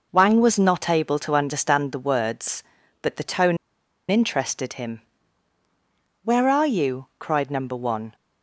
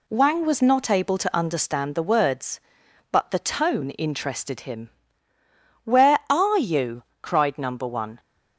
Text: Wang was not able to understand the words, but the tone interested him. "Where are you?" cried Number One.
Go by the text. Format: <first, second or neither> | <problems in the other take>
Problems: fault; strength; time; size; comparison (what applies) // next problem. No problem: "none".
second | pauses between "tone" and "interested"; noticeable; at 3.5 s; 0.53 s long